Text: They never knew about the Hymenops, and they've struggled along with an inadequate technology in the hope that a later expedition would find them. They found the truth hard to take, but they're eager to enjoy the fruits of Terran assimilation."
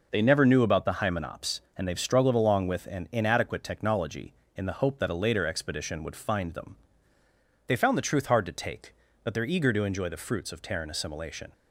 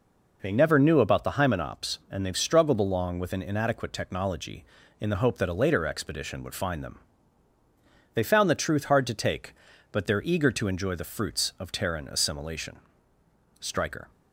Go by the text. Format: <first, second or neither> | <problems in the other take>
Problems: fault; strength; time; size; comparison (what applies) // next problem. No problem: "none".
first | goes on to say "Stryker"; from 13.6 s on; 0.50 s long